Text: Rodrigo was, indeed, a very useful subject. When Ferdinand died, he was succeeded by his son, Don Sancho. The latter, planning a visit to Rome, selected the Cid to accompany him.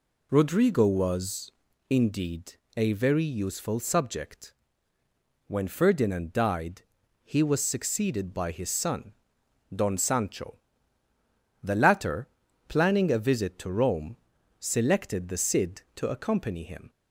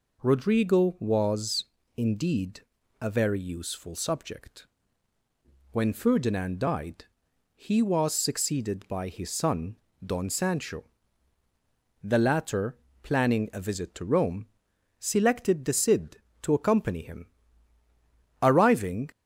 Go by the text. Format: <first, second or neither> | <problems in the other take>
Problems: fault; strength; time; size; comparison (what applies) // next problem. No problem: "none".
first | goes on to say "Arriving"; noticeable; from 18.4 s on; 0.68 s long